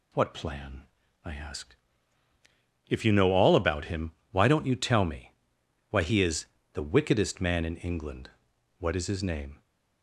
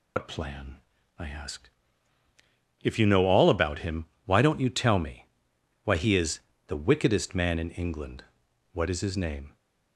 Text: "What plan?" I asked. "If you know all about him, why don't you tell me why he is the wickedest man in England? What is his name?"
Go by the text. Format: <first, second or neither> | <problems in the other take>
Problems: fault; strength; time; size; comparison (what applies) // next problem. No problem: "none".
first | loses the start of "What"; at 0.1 s; 85 ms // pauses between "me" and "why"; noticeable; at 5.2 s; 0.58 s long; noticeable in the first // pauses between "is" and "the"; slight; at 6.4 s; 0.26 s long; slight in the first